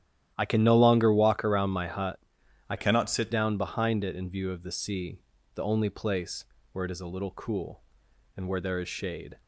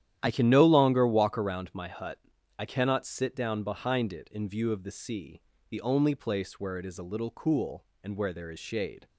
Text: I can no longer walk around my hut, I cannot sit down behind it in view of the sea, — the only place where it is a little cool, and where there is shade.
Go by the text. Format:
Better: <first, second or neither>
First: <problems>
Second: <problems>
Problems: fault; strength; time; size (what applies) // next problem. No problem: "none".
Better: second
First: starts louder than the rest; strong; until 1.3 s; 11.5 dB // changes voice from "cannot" to "sit"; from 2.7 to 3.2 s; 0.5 s long // pauses between "place" and "where"; slight; at 6.4 s; 0.26 s long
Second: starts louder than the rest; strong; until 1.2 s; 11 dB